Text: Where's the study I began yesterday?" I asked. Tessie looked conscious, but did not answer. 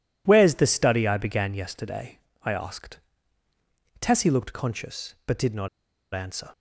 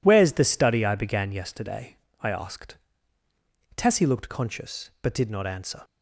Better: second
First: pauses between "not" and "answer"; at 5.6 s; 0.45 s long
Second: none

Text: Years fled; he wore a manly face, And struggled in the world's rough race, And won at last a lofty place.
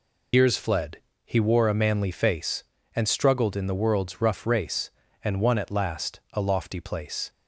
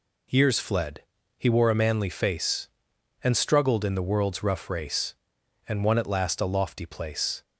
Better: second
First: loses the start of "Years"; at 0.3 s; 90 ms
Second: none

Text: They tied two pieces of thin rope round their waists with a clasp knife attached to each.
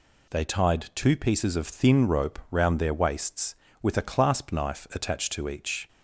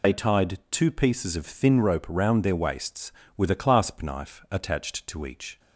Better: first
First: none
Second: loses the start of "They"; at 0.0 s; 60 ms

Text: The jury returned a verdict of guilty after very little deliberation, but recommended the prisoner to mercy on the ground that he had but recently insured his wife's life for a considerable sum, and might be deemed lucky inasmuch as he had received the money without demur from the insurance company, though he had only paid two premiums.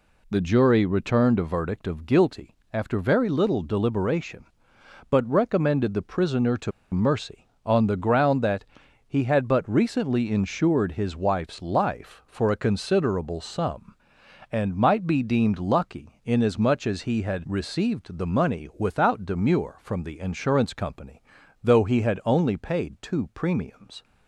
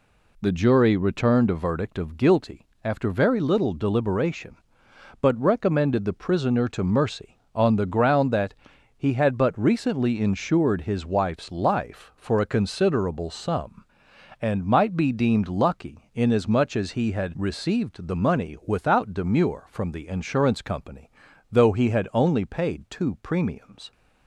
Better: second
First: pauses between "guilty" and "after"; slight; at 2.5 s; 0.18 s long // pauses between "to" and "mercy"; slight; at 6.7 s; 0.22 s long // pauses between "that" and "he"; at 8.6 s; 0.44 s long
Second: pauses between "guilty" and "after"; slight; at 2.6 s; 0.18 s long // pauses between "that" and "he"; at 8.5 s; 0.44 s long

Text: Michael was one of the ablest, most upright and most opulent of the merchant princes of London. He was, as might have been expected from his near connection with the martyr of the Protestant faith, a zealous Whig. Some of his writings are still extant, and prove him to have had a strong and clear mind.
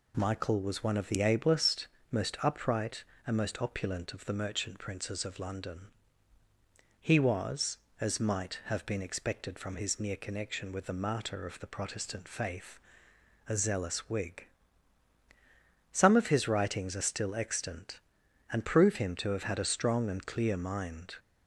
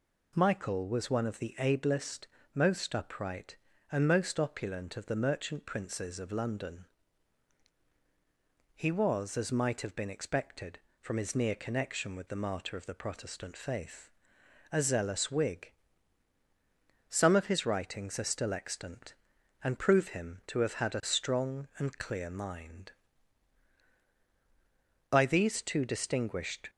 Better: first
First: none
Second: goes on to say "By these two distinguished"; from 25.0 s on; 1.6 s long

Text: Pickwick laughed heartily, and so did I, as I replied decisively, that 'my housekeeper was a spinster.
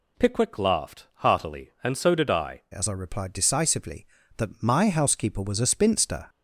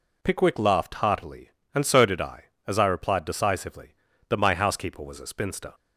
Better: second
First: changes voice at "as"; from 2.7 s on; 3.5 s long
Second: none

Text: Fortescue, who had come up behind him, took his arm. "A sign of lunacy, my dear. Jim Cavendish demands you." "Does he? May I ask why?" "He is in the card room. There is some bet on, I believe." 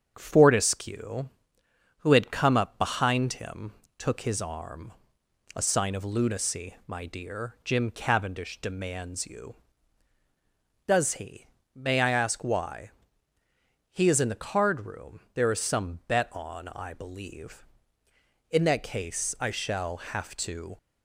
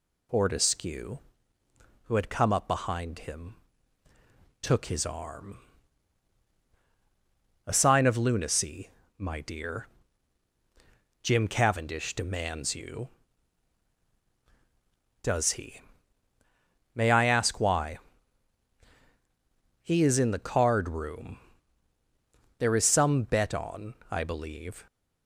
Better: second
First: starts louder than the rest; strong; until 1.1 s; 7.5 dB // goes on to say "In that case I shall have to"; strong; from 18.5 s on; 2.2 s long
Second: none

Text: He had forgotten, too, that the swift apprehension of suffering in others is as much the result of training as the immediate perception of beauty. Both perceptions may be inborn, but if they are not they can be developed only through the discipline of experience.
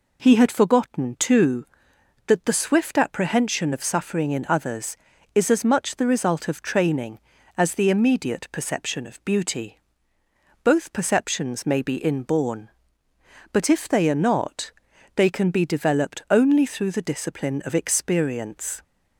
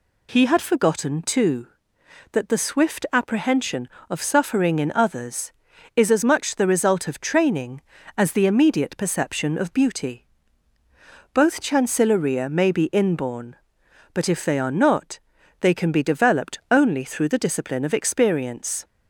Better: first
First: pauses between "not" and "they"; at 14.7 s; 0.44 s long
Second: says "chancilleria" for "perceptions"; at 11.6 s // pauses between "not" and "they"; at 15.1 s; 0.42 s long

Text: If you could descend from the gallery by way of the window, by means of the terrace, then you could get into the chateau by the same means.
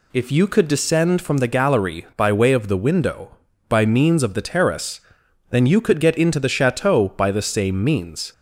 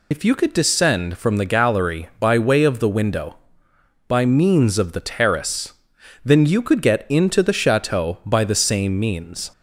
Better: first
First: none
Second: loses the start of "If"; at 0.1 s; 50 ms

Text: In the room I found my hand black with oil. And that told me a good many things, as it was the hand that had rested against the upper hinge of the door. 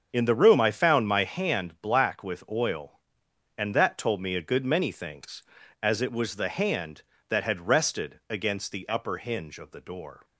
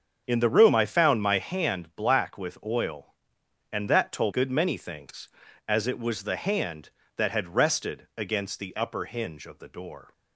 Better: first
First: starts louder than the rest; until 1.1 s; 6.5 dB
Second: starts louder than the rest; until 1.2 s; 7 dB // skips "me a"; at 4.3 s

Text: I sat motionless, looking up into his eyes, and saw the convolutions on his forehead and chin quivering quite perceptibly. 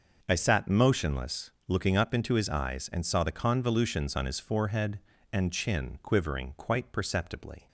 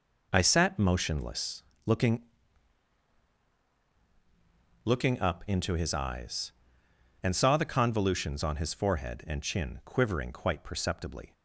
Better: first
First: none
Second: says "looking" twice; at 4.8 s

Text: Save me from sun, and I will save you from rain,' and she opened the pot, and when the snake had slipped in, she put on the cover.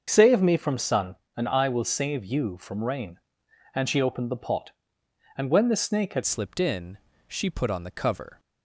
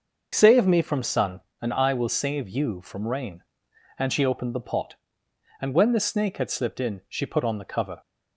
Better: second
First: starts louder than the rest; until 1.0 s; 6.5 dB // changes voice at "slipped"; from 6.2 s on; 2.1 s long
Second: none

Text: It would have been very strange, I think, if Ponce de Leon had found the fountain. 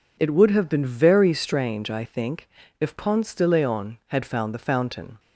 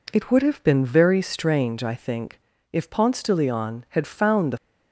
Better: first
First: none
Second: stops before "fountain"; at 4.5 s

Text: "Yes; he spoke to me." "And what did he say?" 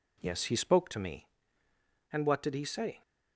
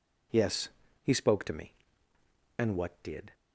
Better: first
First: none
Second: stops before "he say"; at 3.3 s

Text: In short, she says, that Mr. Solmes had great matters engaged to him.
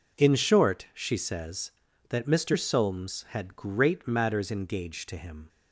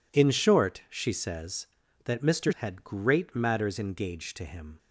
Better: first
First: none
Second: skips "Solmes"; at 2.5 s

